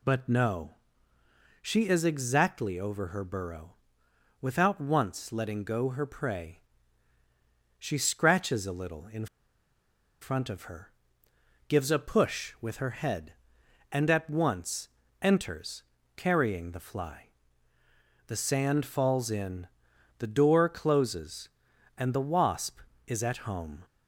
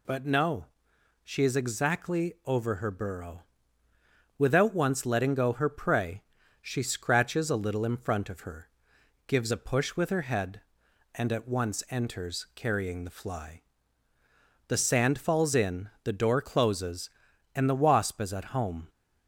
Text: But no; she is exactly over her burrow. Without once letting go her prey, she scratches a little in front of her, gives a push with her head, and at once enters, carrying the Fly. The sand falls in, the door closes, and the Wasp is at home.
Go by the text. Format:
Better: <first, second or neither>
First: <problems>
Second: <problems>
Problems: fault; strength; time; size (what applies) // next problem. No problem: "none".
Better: second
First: pauses between "in" and "front"; noticeable; at 9.2 s; 0.95 s long // pauses between "once" and "enters"; slight; at 14.8 s; 0.34 s long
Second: none